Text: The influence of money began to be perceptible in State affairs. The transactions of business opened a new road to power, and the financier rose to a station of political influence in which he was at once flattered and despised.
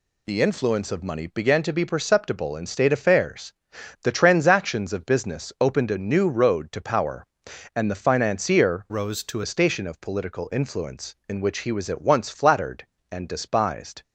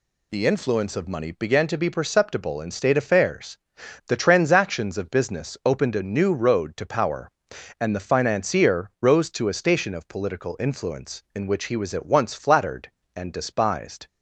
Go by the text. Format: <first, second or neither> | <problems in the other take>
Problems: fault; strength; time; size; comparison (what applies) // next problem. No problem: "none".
second | changes voice from "rose" to "to"; from 8.8 to 9.4 s; 0.6 s long